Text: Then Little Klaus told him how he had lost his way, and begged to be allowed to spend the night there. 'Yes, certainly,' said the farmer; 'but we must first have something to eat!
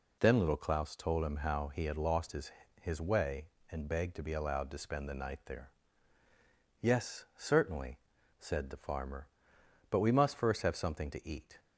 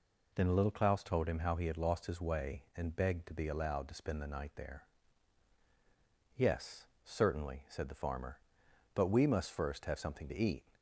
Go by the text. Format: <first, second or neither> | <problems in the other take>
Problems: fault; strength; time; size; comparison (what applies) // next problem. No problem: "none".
second | says "his" twice; at 2.8 s